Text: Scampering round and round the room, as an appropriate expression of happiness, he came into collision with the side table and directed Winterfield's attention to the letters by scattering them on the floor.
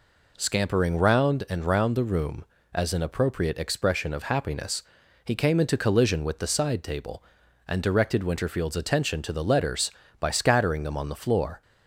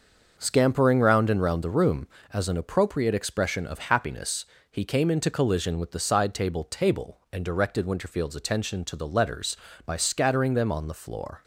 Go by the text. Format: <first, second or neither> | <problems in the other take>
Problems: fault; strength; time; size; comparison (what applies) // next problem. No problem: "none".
first | starts louder than the rest; until 1.3 s; 6 dB // says "table" twice; at 6.6 s